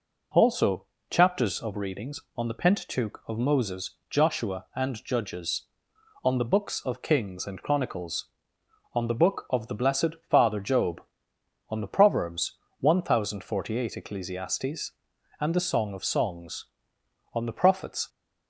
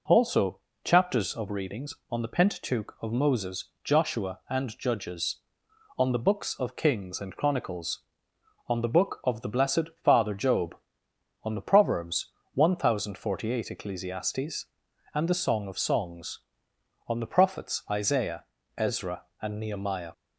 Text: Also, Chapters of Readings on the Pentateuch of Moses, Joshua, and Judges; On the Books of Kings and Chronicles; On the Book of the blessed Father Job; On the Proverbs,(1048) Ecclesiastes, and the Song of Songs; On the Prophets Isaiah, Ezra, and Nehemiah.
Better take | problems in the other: second | pauses between "blessed" and "Father"; slight; at 10.1 s; 0.16 s long; slight in the second // stops before "Isaiah Ezra and Nehemiah"; at 18.0 s

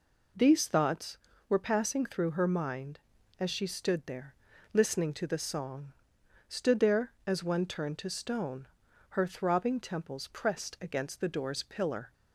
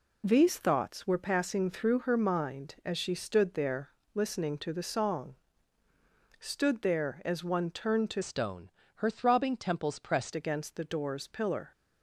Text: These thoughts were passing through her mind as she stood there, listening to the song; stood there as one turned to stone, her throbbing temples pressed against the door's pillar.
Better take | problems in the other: first | changes voice from "stone" to "pressed"; from 8.2 to 10.3 s; 2.1 s long

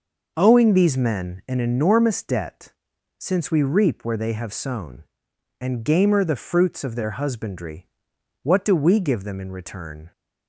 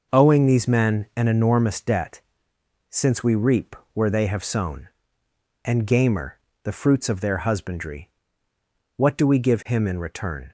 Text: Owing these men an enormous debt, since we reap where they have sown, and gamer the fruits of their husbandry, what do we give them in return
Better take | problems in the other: first | pauses between "reap" and "where"; slight; at 3.7 s; 0.18 s long // pauses between "gamer" and "the"; slight; at 6.3 s; 0.24 s long // says "him" for "them"; at 9.6 s

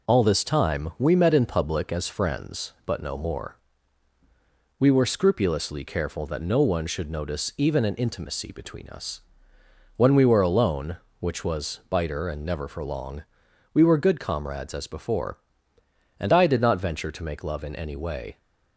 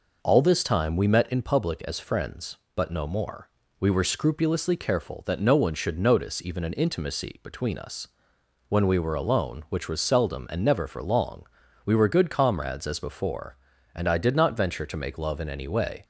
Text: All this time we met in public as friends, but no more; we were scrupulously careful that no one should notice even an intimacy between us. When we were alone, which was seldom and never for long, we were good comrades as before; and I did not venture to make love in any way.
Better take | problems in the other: second | says "biter" for "seldom"; at 11.8 s

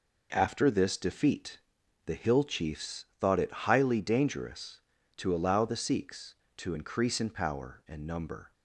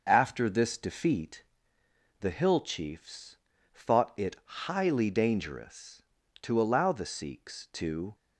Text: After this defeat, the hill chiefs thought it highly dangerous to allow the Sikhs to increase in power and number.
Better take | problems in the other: first | pauses between "chiefs" and "thought"; at 3.3 s; 0.38 s long // stops before "increase in power and number"; at 8.1 s

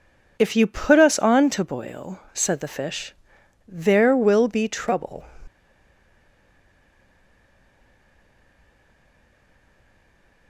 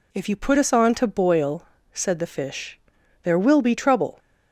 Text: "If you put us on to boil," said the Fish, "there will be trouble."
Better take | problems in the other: second | stays silent after the last word; strong; from 5.4 s on; 5.0 s long

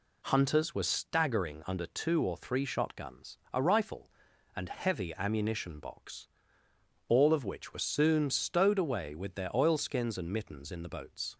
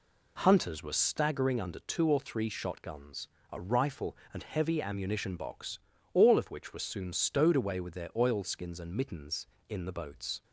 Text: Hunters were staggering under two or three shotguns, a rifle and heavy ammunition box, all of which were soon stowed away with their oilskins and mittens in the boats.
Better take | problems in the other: neither | none

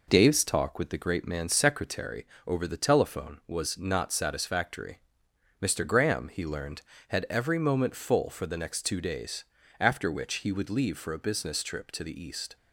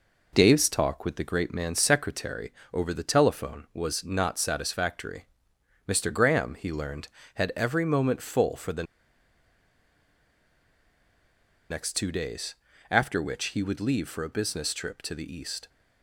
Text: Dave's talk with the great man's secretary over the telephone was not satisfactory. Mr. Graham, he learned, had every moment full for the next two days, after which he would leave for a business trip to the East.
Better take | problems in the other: first | pauses between "secretary" and "over"; slight; at 2.5 s; 0.20 s long; slight in the first // pauses between "the" and "next"; strong; at 8.8 s; 2.8 s long

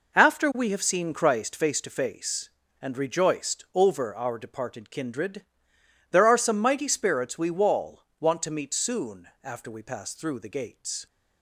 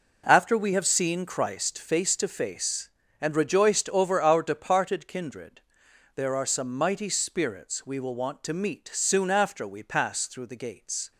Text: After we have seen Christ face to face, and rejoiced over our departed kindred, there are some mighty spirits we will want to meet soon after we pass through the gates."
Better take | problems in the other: second | says "wall" for "will"; at 7.5 s

